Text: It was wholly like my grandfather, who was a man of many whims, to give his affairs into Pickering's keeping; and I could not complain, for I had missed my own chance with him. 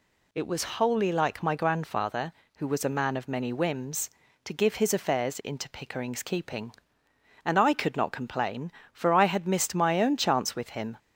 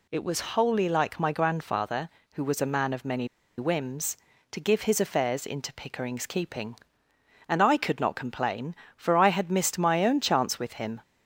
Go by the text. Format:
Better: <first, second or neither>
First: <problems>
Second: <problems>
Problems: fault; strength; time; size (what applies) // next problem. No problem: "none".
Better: first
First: none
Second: pauses between "many" and "whims"; slight; at 3.2 s; 0.30 s long